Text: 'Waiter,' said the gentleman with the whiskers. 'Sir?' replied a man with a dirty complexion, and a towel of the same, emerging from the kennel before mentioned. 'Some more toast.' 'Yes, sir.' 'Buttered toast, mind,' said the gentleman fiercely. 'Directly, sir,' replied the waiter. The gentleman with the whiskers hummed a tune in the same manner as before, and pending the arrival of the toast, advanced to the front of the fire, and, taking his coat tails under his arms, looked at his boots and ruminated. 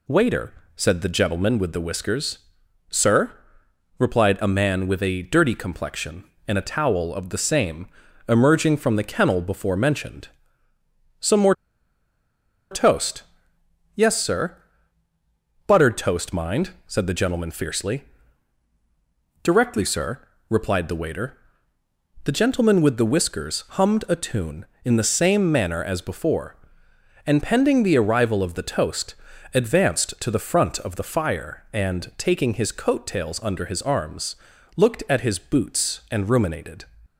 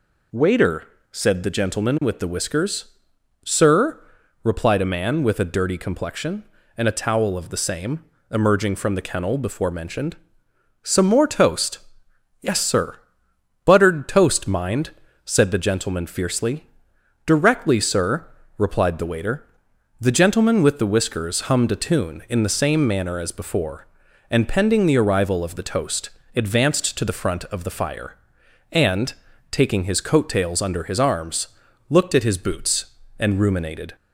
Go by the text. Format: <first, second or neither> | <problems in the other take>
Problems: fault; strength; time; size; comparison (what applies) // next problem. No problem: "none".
second | pauses between "more" and "toast"; at 11.5 s; 1.1 s long